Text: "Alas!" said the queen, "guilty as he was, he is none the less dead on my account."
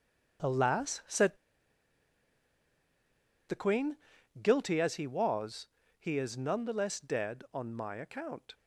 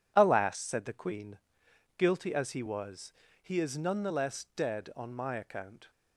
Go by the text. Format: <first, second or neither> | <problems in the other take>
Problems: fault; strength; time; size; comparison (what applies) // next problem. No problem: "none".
second | starts louder than the rest; until 3.5 s; 6.5 dB // pauses between "said" and "the"; strong; at 1.3 s; 2.1 s long